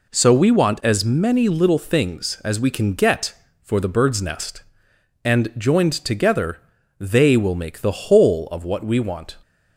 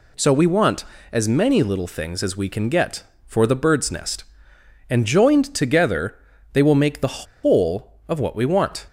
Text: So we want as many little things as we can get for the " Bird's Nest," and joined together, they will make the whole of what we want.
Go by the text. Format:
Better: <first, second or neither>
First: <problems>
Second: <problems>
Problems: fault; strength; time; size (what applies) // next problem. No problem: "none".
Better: first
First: none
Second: pauses between "the" and "whole"; slight; at 7.2 s; 0.18 s long